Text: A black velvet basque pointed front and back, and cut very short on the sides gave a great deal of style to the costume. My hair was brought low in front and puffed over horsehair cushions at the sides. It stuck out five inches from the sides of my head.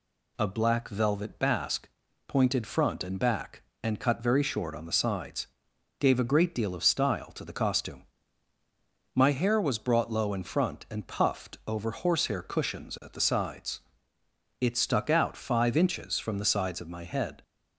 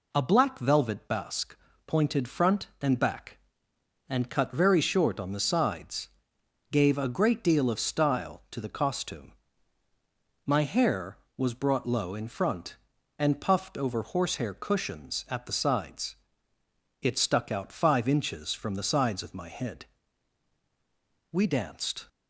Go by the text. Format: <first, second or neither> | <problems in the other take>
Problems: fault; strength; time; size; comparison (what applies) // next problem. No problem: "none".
first | pauses between "basque" and "pointed"; slight; at 1.5 s; 0.30 s long; also in the first // pauses between "sides" and "gave"; noticeable; at 6.0 s; 0.64 s long; noticeable in the first // goes on to say "We danced"; noticeable; from 21.3 s on; 0.76 s long